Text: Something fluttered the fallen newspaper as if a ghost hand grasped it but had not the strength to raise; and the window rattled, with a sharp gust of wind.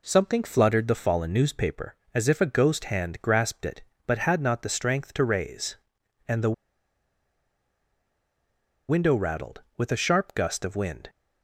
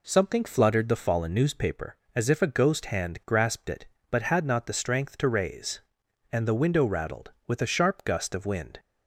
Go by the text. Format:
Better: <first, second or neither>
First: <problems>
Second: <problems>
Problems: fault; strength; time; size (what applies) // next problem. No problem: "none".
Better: second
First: pauses between "the" and "window"; strong; at 6.5 s; 2.3 s long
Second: none